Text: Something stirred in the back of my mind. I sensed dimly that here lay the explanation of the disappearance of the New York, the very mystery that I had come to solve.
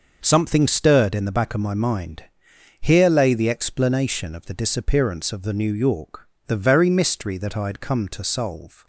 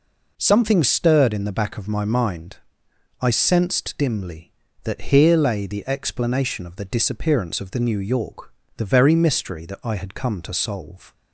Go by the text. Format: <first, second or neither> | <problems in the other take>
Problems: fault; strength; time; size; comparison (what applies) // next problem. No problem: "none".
second | skips "I sensed dimly that"; at 2.5 s